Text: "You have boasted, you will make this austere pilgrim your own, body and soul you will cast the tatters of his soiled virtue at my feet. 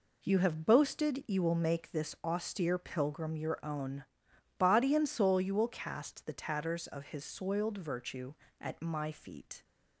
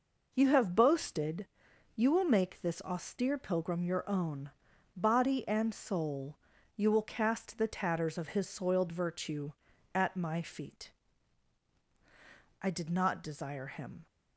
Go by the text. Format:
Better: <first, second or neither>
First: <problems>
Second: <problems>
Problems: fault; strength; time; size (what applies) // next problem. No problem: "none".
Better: first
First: none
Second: pauses between "soul" and "you"; slight; at 6.3 s; 0.36 s long // goes on to say "I did not desire him"; from 12.6 s on; 1.4 s long